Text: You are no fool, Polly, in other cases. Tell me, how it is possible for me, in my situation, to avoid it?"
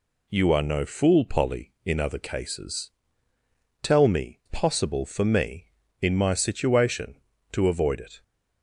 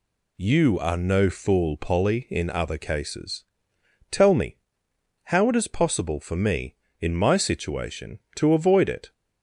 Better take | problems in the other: second | skips "how it is"; at 4.4 s

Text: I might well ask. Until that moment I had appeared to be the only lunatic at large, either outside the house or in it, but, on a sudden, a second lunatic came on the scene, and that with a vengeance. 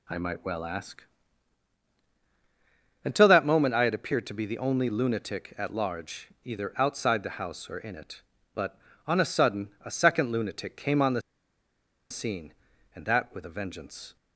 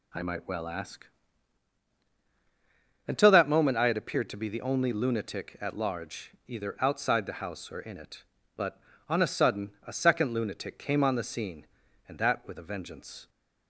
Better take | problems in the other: second | pauses between "the" and "scene"; noticeable; at 11.2 s; 0.89 s long

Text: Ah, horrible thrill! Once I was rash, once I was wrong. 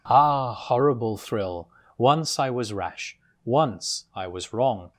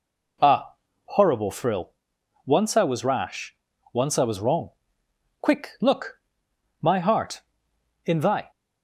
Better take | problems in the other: first | goes on to say "Quick look My heart in thy"; strong; from 5.4 s on; 3.1 s long

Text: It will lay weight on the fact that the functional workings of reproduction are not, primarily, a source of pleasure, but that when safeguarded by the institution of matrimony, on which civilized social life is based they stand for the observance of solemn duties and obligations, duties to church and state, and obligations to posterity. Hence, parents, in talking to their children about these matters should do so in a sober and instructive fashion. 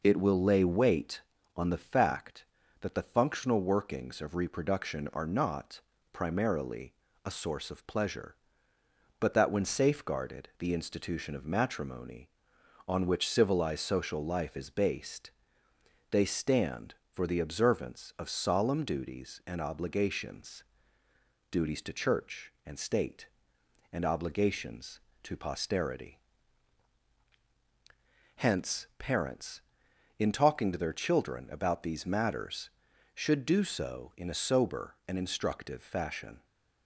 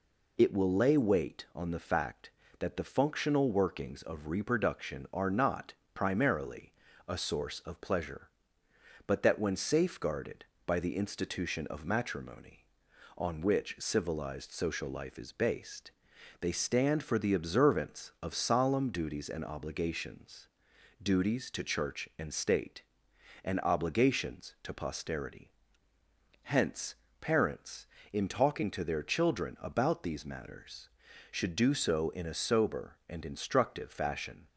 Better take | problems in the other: second | skips "by"; at 10.5 s // pauses between "based" and "they"; noticeable; at 15.3 s; 0.80 s long; noticeable in the second

